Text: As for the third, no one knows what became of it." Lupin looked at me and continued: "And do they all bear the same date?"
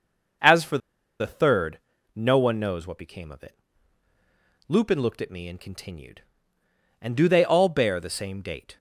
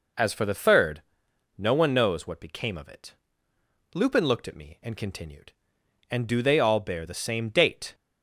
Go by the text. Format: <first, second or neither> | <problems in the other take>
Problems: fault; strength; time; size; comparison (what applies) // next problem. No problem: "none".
second | pauses between "for" and "the"; at 0.7 s; 0.42 s long